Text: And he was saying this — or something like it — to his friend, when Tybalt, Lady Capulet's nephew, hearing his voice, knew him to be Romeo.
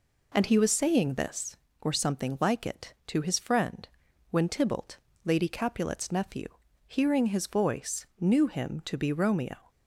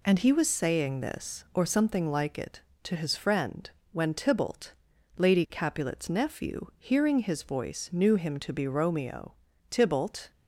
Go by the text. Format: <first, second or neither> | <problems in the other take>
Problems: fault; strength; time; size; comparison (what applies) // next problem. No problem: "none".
first | goes on to say "Tybalt"; from 9.7 s on; 0.60 s long